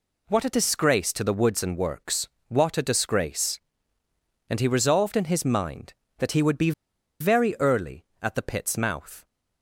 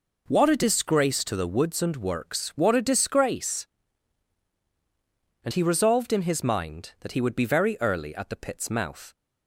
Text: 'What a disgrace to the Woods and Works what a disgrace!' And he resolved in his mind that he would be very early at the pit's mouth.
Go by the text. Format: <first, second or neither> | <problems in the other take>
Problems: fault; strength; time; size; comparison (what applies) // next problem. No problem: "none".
second | pauses between "Works" and "what"; slight; at 2.2 s; 0.20 s long // pauses between "be" and "very"; noticeable; at 6.7 s; 0.49 s long